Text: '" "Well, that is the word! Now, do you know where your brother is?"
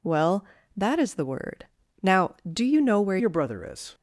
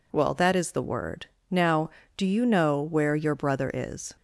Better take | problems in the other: second | changes voice at "your"; from 3.1 s on; 0.8 s long

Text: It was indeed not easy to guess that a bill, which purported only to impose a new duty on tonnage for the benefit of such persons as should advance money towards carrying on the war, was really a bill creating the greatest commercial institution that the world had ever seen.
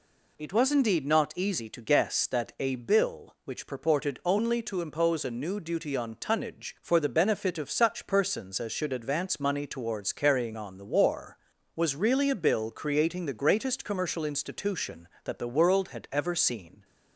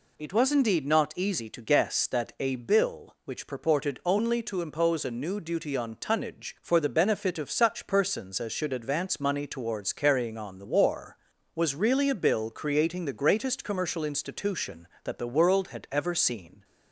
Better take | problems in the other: neither | none

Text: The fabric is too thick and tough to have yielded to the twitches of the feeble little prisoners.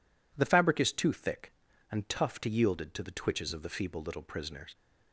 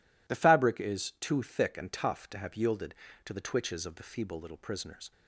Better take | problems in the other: second | skips "have"; at 2.4 s

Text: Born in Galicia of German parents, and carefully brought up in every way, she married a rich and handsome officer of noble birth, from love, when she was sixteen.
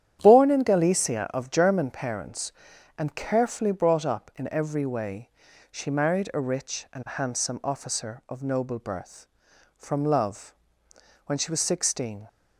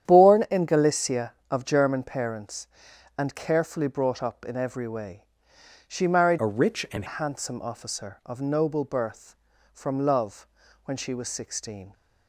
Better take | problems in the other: first | starts louder than the rest; strong; until 1.1 s; 10 dB; strong in the first // changes voice from "a" to "and"; from 6.3 to 7.0 s; 0.7 s long

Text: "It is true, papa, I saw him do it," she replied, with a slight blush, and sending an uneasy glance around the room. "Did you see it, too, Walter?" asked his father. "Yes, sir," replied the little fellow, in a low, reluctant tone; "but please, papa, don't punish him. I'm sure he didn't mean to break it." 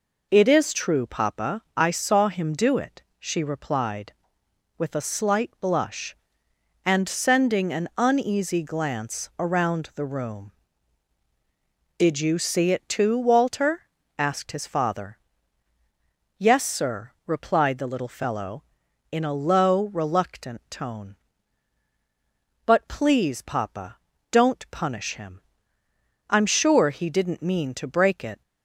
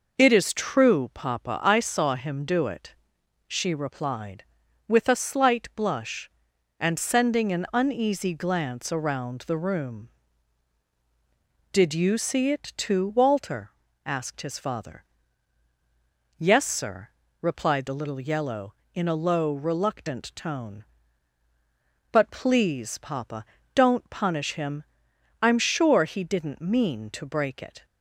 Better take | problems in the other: first | says "yellow" for "fellow"; at 18.1 s

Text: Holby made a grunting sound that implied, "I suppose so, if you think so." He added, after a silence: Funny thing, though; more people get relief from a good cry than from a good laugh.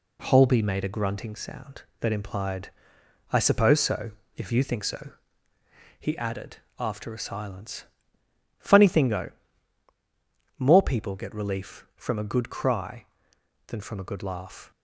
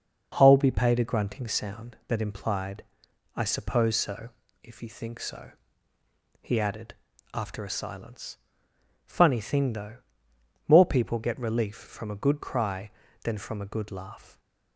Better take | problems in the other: first | says "paid" for "made"; at 0.7 s

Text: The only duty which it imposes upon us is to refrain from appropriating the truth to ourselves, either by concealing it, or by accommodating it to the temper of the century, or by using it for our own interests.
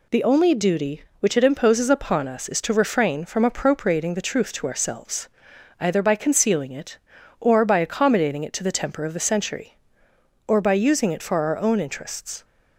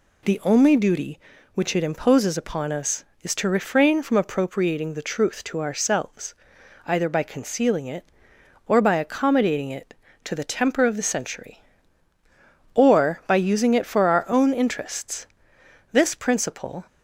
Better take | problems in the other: first | goes on to say "This principle"; noticeable; from 15.9 s on; 0.94 s long

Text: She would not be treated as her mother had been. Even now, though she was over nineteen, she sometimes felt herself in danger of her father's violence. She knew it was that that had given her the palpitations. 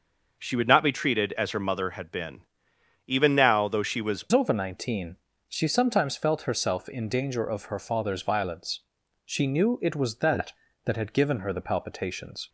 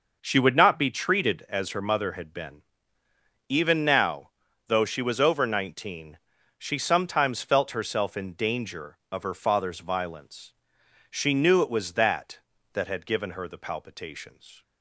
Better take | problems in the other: second | changes voice at "over"; from 4.3 s on; 8.1 s long

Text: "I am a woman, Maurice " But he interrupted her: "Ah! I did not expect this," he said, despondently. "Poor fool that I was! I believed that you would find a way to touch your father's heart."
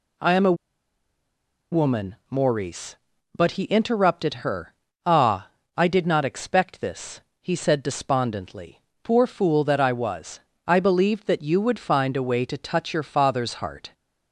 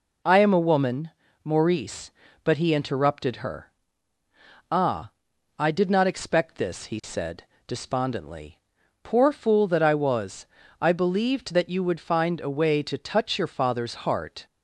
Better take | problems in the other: second | pauses between "a" and "woman"; at 0.5 s; 1.1 s long

